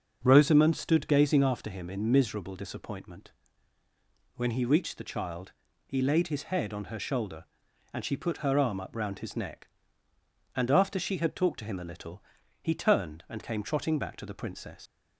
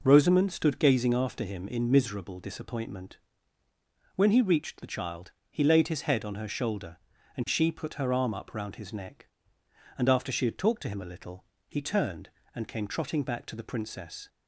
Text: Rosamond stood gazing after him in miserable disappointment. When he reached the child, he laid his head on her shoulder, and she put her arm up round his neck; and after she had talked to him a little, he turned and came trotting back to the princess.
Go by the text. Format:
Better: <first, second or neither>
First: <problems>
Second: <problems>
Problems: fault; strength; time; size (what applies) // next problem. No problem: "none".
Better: second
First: starts louder than the rest; until 1.2 s; 6.5 dB // leaves "princess" unfinished; at 14.8 s; 90 ms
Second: none